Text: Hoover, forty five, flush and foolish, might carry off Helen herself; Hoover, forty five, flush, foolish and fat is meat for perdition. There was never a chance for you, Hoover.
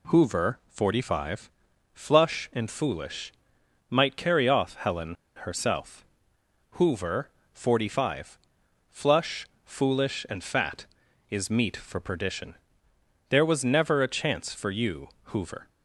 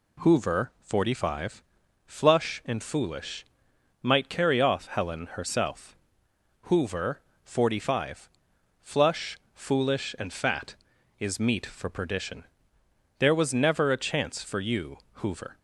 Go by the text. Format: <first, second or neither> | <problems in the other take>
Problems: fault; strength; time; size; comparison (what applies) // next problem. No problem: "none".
second | pauses between "Helen" and "herself"; slight; at 5.1 s; 0.26 s long